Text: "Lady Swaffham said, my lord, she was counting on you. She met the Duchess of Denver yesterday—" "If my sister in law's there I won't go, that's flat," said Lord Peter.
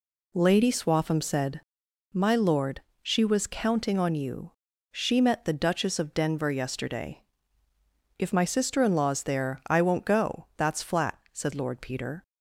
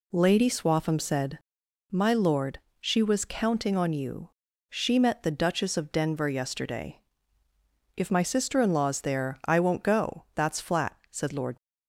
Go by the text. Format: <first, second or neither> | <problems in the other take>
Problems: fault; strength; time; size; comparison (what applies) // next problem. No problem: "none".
first | stops before "Peter"; at 11.5 s